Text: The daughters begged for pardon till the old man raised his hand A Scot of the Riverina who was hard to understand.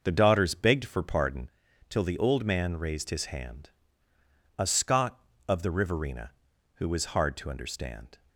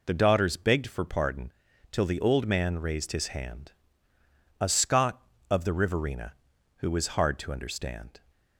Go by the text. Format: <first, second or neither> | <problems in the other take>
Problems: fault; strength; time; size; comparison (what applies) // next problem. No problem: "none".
second | starts louder than the rest; noticeable; until 1.6 s; 6 dB // pauses between "pardon" and "till"; at 1.4 s; 0.38 s long; also in the second // pauses between "hand" and "A"; noticeable; at 3.6 s; 0.88 s long; noticeable in the second